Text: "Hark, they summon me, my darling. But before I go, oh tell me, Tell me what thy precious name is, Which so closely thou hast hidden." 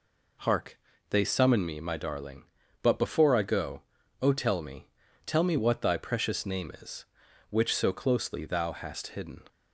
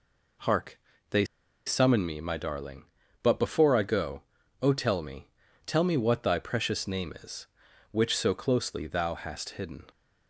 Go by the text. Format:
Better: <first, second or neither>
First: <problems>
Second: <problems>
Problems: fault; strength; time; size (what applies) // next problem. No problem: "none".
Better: first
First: none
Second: pauses between "they" and "summon"; at 1.2 s; 0.41 s long